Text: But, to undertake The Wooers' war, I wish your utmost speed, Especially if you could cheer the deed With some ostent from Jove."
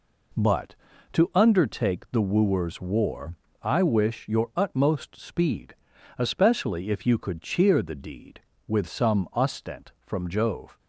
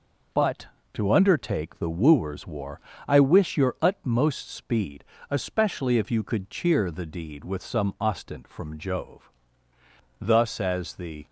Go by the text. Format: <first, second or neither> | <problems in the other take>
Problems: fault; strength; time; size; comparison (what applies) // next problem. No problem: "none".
first | goes on to say "Thus as the"; noticeable; from 10.1 s on; 1.0 s long